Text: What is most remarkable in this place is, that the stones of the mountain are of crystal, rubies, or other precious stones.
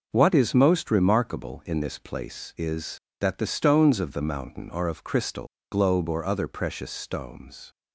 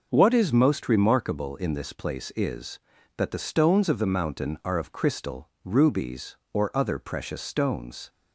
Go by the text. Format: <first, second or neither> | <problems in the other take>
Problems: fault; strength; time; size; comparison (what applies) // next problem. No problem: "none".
second | says "globe" for "rubies"; at 5.7 s